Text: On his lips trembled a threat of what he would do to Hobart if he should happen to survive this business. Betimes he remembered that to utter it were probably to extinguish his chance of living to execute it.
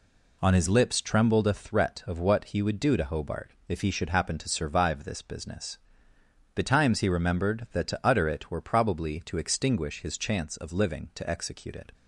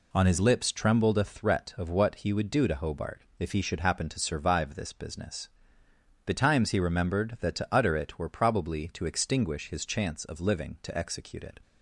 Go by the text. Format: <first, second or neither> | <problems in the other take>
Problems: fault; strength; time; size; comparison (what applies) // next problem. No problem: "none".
neither | pauses between "Hobart" and "if"; slight; the same in both